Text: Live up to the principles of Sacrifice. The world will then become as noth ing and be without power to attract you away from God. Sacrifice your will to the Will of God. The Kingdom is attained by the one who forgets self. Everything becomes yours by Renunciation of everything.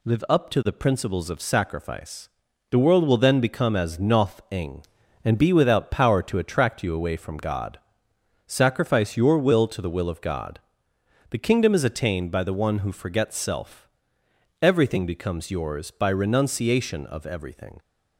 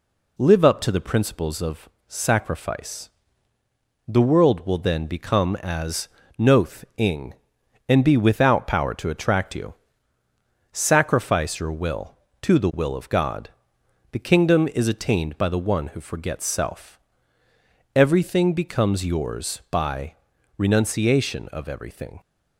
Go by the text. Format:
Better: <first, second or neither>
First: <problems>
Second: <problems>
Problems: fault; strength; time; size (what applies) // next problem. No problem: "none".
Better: first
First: none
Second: pauses between "of" and "Sacrifice"; slight; at 1.8 s; 0.20 s long // pauses between "as" and "noth"; slight; at 6.0 s; 0.28 s long // skips "away from God"; at 10.2 s // pauses between "by" and "Renunciation"; at 20.1 s; 0.42 s long